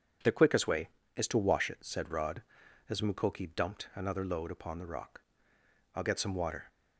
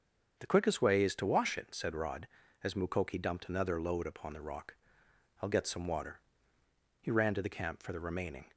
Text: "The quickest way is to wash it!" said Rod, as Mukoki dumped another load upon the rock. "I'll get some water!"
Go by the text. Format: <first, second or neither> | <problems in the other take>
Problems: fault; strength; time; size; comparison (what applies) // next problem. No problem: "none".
first | starts louder than the rest; strong; until 1.4 s; 7 dB // goes on to say "He ran to the camp for the remaining"; from 6.9 s on; 1.5 s long